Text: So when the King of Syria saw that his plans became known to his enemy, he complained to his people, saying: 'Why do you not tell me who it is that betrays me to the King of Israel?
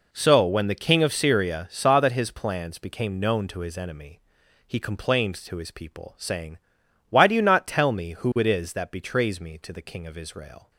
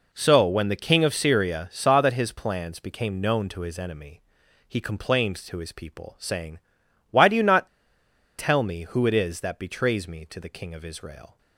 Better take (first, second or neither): first